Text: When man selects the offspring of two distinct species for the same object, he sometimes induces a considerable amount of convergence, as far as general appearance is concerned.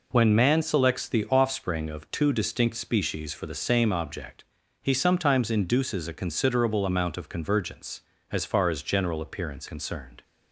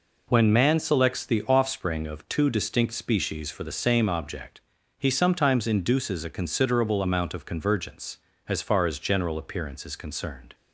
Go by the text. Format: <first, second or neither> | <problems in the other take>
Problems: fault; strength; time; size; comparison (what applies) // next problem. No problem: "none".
second | skips "is"; at 9.6 s